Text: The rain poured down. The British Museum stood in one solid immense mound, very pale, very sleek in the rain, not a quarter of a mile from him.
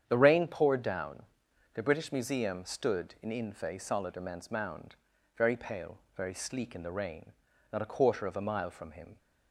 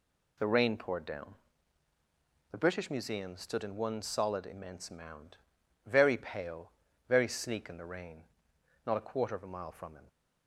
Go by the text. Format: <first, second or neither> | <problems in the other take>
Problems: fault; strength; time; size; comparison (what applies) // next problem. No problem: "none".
second | starts louder than the rest; strong; until 1.0 s; 8.5 dB // says "infe" for "one"; at 3.3 s